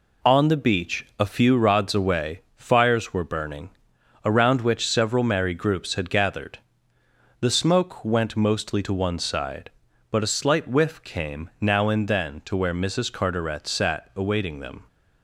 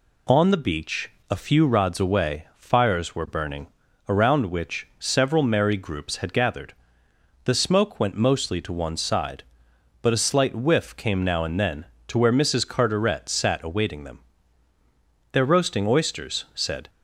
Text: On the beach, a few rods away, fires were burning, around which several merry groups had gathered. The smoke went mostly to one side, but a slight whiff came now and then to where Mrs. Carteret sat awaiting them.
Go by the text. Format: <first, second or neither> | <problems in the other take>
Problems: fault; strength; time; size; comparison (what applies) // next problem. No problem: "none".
first | goes on to say "They're roasting oysters said"; from 15.3 s on; 1.5 s long